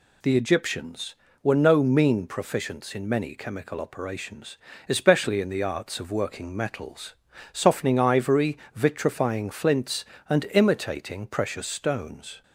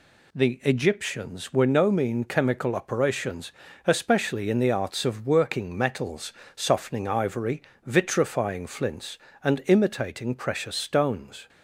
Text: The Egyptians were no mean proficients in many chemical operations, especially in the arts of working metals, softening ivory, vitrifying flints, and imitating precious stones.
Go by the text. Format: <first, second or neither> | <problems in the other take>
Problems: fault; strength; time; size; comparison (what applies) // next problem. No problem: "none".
first | skips "proficients in many"; at 2.2 s